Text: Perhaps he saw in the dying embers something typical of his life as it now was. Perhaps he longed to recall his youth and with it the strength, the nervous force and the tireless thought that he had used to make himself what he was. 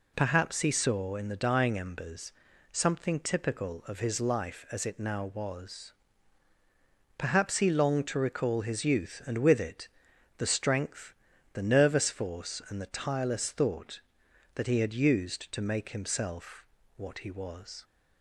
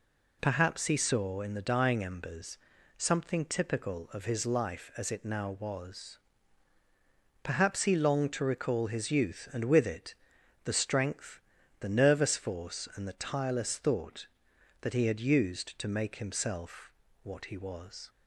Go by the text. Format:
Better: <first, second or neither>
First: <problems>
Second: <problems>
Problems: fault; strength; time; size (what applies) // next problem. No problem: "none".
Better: neither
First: pauses between "embers" and "something"; at 2.3 s; 0.40 s long // pauses between "it" and "the"; noticeable; at 9.8 s; 0.50 s long // pauses between "himself" and "what"; slight; at 16.6 s; 0.32 s long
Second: pauses between "embers" and "something"; at 2.5 s; 0.40 s long // pauses between "it" and "the"; noticeable; at 10.1 s; 0.50 s long // pauses between "himself" and "what"; slight; at 16.9 s; 0.32 s long